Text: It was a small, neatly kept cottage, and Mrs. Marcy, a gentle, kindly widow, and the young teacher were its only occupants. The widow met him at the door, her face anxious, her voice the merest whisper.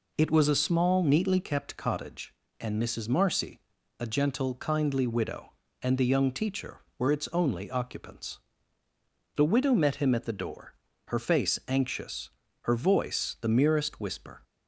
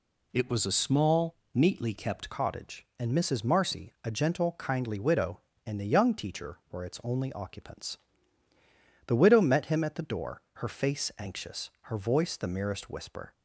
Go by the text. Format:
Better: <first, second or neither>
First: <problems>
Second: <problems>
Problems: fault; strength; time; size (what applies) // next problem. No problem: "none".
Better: first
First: none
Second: changes voice at "cottage"; from 2.2 s on; 11.1 s long